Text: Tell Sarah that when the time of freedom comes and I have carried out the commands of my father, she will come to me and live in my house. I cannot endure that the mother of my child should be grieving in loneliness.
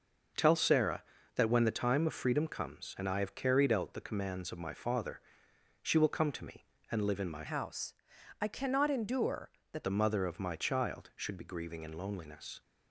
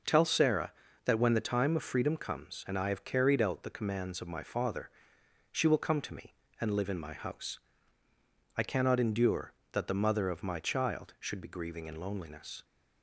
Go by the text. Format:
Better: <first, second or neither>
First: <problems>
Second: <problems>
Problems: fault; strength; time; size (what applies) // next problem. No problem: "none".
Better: second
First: changes voice from "house" to "that"; from 7.4 to 9.8 s; 2.4 s long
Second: none